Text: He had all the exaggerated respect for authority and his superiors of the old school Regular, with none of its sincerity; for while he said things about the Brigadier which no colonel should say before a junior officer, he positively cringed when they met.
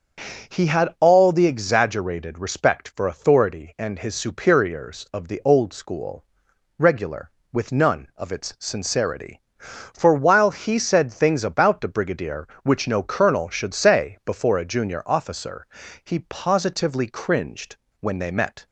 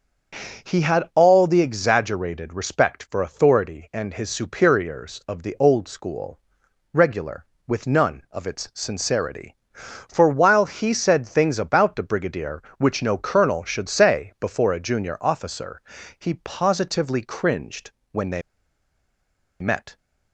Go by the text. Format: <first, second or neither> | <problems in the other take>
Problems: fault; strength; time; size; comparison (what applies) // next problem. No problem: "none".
first | starts louder than the rest; until 1.7 s; 7 dB; also in the first // pauses between "school" and "Regular"; noticeable; at 6.3 s; 0.52 s long; noticeable in the first // pauses between "cringed" and "when"; slight; at 17.9 s; 0.18 s long; slight in the first // pauses between "they" and "met"; at 18.4 s; 1.1 s long